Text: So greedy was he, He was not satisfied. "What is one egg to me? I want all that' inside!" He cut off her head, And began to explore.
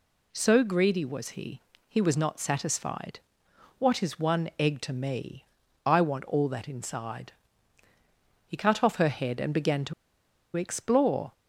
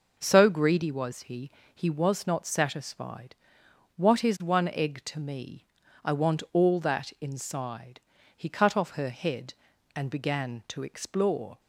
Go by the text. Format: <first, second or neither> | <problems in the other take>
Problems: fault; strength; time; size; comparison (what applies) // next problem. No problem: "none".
second | pauses between "to" and "explore"; noticeable; at 9.9 s; 0.62 s long